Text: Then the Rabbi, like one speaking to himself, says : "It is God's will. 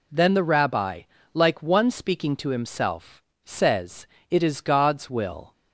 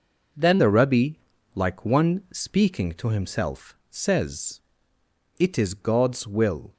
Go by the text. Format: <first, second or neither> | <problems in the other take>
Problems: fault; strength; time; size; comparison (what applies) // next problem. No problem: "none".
first | changes voice at "the"; from 0.5 s on; 6.2 s long